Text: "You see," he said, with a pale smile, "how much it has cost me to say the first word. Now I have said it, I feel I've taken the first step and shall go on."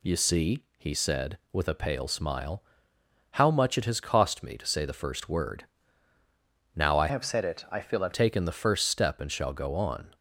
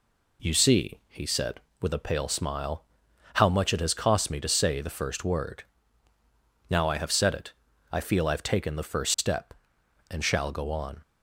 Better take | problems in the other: second | changes voice from "have" to "I've"; from 7.1 to 8.1 s; 1.0 s long

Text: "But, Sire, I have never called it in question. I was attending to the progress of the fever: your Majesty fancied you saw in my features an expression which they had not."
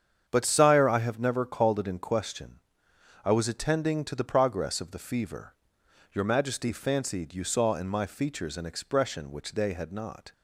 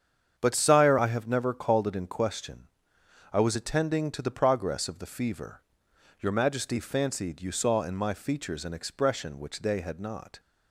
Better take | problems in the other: neither | starts louder than the rest; strong; the same in both

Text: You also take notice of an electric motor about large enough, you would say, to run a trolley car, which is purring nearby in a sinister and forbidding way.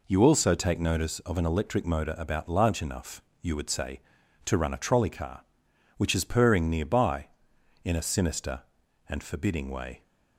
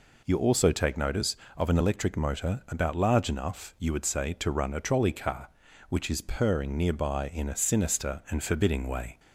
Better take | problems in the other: neither | none

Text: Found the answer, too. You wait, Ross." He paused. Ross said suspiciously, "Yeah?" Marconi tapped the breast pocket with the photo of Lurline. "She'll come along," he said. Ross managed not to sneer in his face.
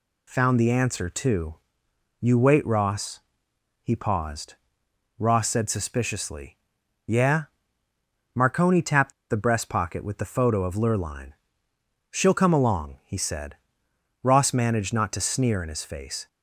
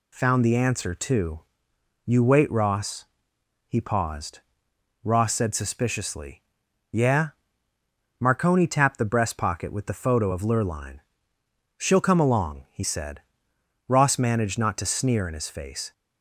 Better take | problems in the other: second | pauses between "tapped" and "the"; slight; at 9.1 s; 0.18 s long

